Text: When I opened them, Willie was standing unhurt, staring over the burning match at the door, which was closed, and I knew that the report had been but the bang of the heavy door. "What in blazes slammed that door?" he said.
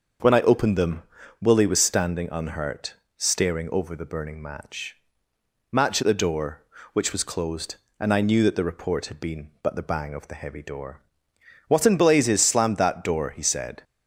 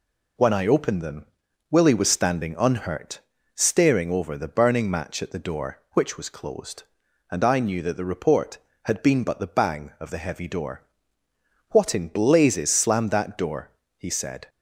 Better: second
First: starts louder than the rest; until 1.6 s; 6.5 dB // says "match" twice; at 5.7 s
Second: none

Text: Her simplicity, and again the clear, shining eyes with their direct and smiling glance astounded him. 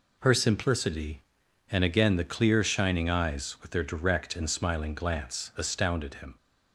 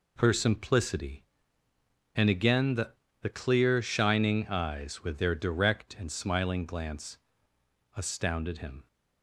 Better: first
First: none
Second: says "the" twice; at 3.2 s // pauses between "glance" and "astounded"; noticeable; at 7.1 s; 0.76 s long

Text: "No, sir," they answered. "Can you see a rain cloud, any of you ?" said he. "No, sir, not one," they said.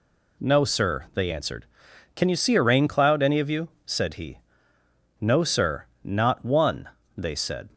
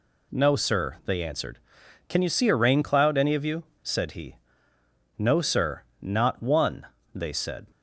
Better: neither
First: none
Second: none

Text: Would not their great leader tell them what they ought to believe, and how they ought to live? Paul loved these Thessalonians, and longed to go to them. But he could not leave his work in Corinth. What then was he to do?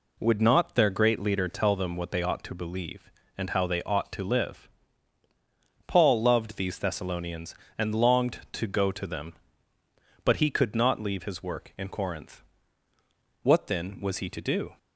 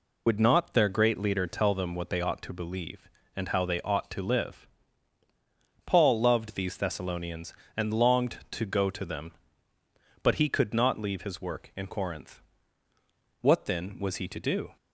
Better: first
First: none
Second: loses the start of "Would"; at 0.2 s; 85 ms

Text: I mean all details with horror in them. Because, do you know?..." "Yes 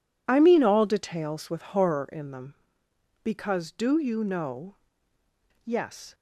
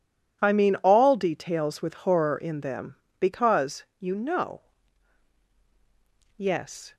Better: first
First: none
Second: skips "do"; at 3.9 s

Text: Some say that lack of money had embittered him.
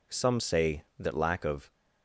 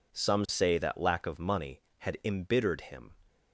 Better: second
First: stops before "money had embittered him"; at 1.7 s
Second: none

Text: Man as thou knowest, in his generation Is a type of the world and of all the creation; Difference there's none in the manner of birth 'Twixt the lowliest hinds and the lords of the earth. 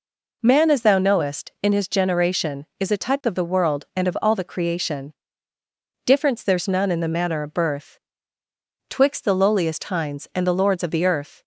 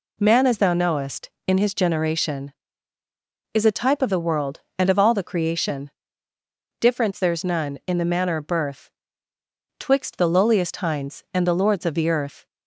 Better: neither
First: pauses between "birth" and "Twixt"; noticeable; at 7.9 s; 0.90 s long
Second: pauses between "birth" and "Twixt"; noticeable; at 8.9 s; 0.90 s long

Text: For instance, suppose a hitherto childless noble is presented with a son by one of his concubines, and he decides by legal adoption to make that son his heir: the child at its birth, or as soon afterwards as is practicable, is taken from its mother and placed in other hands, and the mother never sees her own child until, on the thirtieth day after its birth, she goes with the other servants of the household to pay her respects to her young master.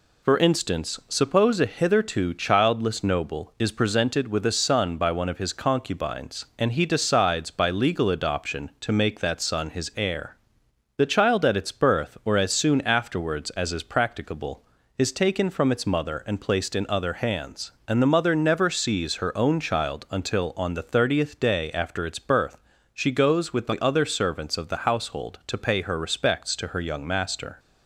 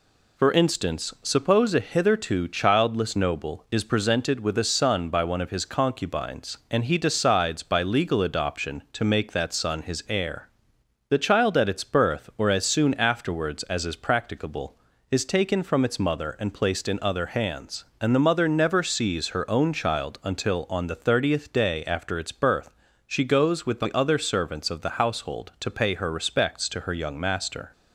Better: neither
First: none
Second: none

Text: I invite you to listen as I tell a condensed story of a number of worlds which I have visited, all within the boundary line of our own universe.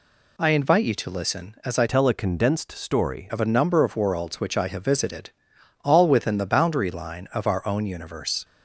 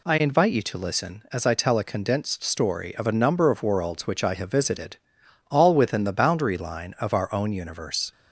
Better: second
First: changes voice from "tell" to "story"; from 1.8 to 3.2 s; 1.4 s long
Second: none

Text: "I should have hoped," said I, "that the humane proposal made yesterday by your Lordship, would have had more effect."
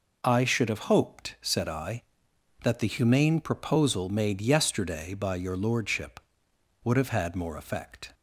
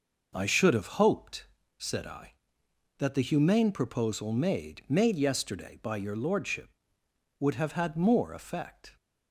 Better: first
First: none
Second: says "made" twice; at 4.8 s

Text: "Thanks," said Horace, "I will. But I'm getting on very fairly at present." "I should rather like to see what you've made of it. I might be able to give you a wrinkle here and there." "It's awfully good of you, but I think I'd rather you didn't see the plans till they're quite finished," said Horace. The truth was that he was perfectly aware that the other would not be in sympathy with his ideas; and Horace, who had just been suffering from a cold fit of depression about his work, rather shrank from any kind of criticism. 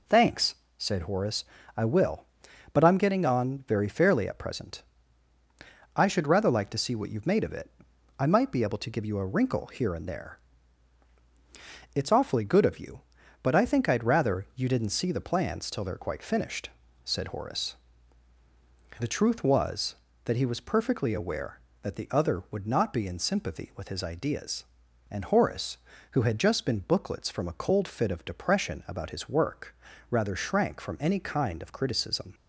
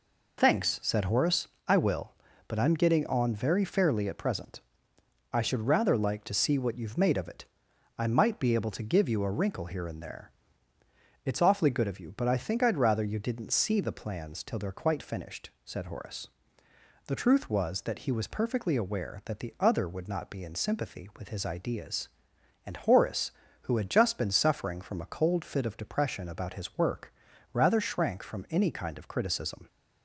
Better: second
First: says "booklets" for "suffering"; at 26.7 s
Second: none

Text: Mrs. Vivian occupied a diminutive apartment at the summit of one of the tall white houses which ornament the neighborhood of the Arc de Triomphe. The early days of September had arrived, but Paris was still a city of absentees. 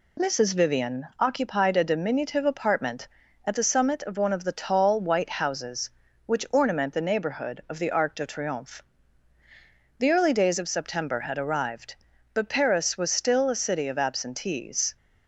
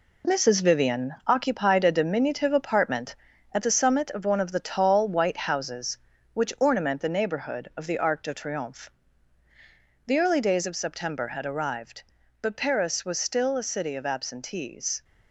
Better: first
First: none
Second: gets quieter; throughout; 7 dB

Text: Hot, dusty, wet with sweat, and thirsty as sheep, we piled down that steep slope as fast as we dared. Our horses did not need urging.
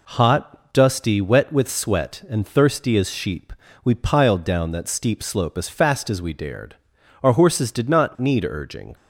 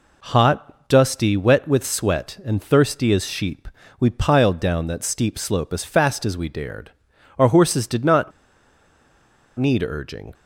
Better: first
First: none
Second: pauses between "not" and "need"; strong; at 8.3 s; 1.2 s long

